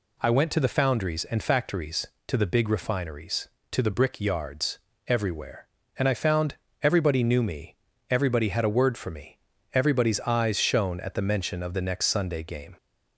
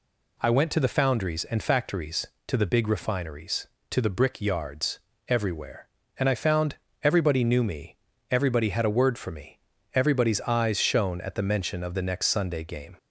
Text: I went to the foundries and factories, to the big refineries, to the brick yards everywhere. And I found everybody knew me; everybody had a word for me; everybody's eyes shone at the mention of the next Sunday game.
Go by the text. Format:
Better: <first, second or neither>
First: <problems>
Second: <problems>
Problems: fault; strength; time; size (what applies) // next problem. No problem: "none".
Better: neither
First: pauses between "yards" and "everywhere"; slight; at 4.7 s; 0.30 s long // pauses between "found" and "everybody"; slight; at 6.5 s; 0.26 s long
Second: pauses between "yards" and "everywhere"; slight; at 4.9 s; 0.30 s long // pauses between "found" and "everybody"; slight; at 6.7 s; 0.26 s long